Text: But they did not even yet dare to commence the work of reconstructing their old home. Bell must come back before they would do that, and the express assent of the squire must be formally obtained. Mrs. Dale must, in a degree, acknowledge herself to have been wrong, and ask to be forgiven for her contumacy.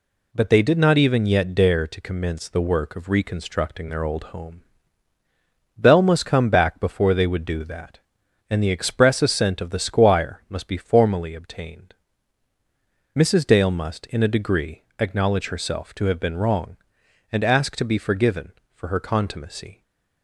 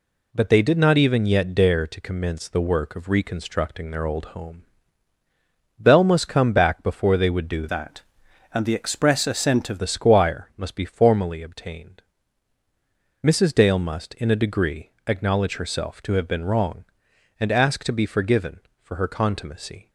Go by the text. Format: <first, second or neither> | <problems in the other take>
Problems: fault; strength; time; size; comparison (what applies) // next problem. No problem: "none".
first | changes voice from "that" to "of"; from 7.6 to 9.8 s; 2.2 s long